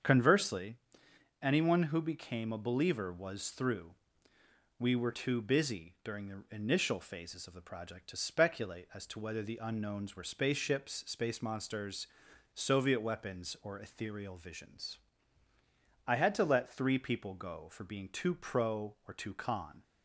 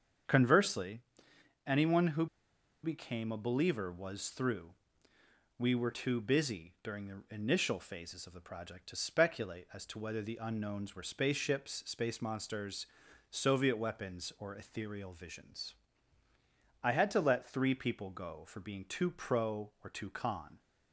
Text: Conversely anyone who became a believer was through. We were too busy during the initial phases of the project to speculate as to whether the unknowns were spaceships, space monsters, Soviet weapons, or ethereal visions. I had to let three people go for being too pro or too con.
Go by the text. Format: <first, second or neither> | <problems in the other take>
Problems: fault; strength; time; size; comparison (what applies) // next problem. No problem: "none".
first | starts louder than the rest; strong; until 1.9 s; 7 dB; also in the first // pauses between "Conversely" and "anyone"; noticeable; at 0.9 s; 0.66 s long; noticeable in the first // pauses between "who" and "became"; noticeable; at 2.2 s; 0.57 s long